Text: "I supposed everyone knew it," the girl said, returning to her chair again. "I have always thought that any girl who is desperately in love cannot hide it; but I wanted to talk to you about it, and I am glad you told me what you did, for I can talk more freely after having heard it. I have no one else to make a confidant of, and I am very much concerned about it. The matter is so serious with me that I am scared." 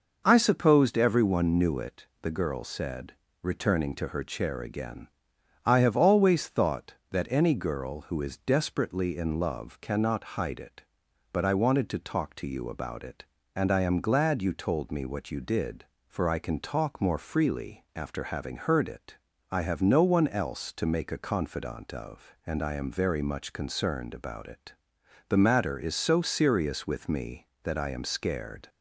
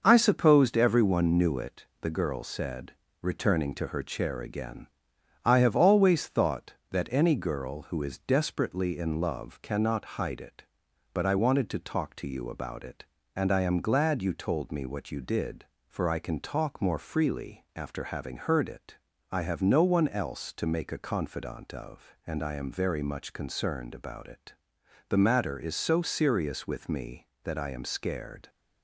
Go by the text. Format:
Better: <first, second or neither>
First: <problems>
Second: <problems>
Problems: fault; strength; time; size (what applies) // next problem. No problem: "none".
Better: first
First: none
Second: gets quieter; noticeable; throughout; 5 dB